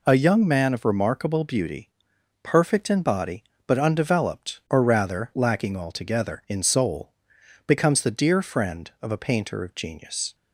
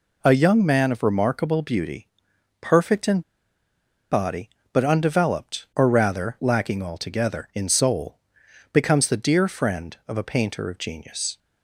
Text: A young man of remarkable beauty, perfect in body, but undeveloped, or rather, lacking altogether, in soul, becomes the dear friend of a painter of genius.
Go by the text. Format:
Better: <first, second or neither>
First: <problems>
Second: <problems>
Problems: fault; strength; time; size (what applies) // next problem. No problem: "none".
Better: first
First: none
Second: pauses between "in" and "body"; noticeable; at 3.2 s; 0.90 s long